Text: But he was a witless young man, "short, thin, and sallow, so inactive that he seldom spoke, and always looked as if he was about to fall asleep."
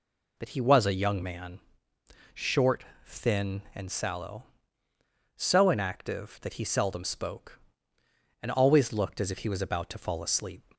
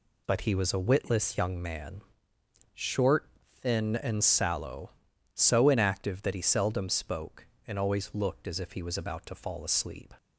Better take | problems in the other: second | skips "witless"; at 0.9 s

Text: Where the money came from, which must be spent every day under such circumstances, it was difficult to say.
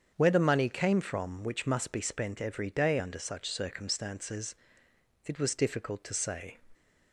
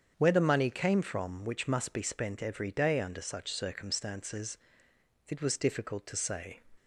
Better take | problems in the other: neither | starts louder than the rest; strong; the same in both

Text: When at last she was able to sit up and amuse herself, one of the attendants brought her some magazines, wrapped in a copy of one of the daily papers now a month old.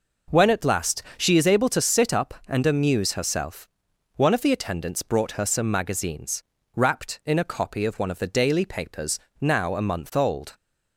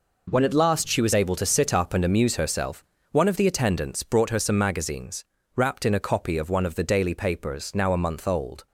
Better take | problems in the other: second | pauses between "last" and "she"; slight; at 1.0 s; 0.16 s long // says "is" for "was"; at 1.3 s // pauses between "papers" and "now"; slight; at 9.1 s; 0.22 s long

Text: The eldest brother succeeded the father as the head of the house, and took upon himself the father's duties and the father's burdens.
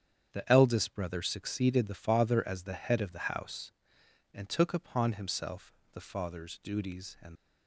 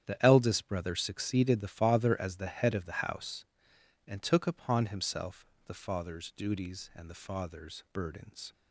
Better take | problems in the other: second | starts louder than the rest; strong; until 1.3 s; 8.5 dB; strong in the second // pauses between "himself" and "the"; slight; at 5.7 s; 0.20 s long; slight in the second // stops before "the father's burdens"; at 7.3 s

